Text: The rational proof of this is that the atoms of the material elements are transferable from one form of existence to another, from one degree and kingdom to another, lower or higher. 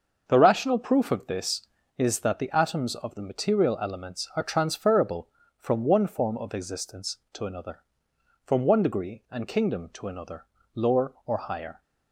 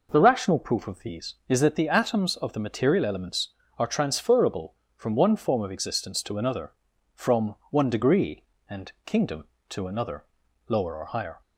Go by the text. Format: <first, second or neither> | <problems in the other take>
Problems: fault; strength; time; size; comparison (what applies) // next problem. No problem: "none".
first | says "these" for "this"; at 0.9 s // pauses between "from" and "one"; slight; at 7.5 s; 0.16 s long // pauses between "and" and "kingdom"; slight; at 8.8 s; 0.16 s long